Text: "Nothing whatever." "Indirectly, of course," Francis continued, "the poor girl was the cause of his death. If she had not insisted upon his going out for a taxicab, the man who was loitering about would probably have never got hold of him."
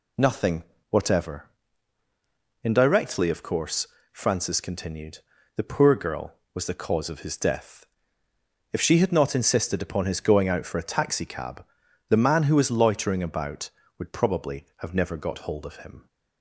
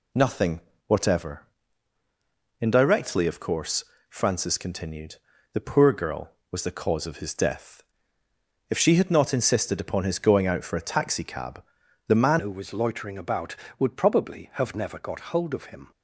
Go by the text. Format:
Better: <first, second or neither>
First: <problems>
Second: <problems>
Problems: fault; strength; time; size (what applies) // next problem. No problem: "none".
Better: first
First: pauses between "Nothing" and "whatever"; slight; at 0.6 s; 0.28 s long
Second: pauses between "Nothing" and "whatever"; slight; at 0.5 s; 0.28 s long // changes voice at "who"; from 12.3 s on; 3.6 s long